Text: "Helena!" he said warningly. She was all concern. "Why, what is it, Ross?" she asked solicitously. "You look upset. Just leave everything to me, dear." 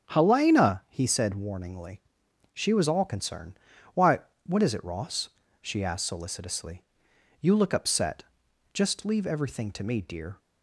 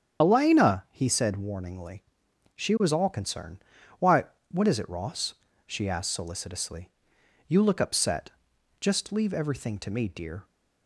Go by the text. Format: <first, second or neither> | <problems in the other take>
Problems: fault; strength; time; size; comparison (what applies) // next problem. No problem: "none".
first | loses the start of "Helena"; at 0.2 s; 115 ms // starts louder than the rest; strong; until 1.2 s; 8.5 dB; also in the first